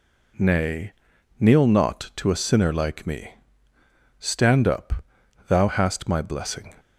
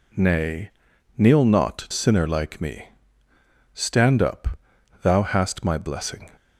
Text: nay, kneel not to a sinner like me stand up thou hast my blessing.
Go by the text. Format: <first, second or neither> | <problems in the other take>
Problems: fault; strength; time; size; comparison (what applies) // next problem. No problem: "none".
first | skips "to a"; at 1.8 s // pauses between "me" and "stand"; noticeable; at 2.8 s; 0.86 s long; noticeable in the first // pauses between "up" and "thou"; noticeable; at 4.5 s; 0.46 s long; noticeable in the first